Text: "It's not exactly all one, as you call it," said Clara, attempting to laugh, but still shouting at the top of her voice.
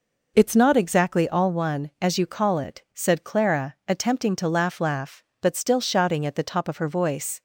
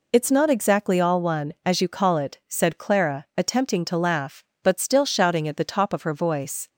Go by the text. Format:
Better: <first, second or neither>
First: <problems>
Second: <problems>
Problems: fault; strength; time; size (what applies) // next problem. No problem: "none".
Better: second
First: says "laugh" twice; at 4.7 s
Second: none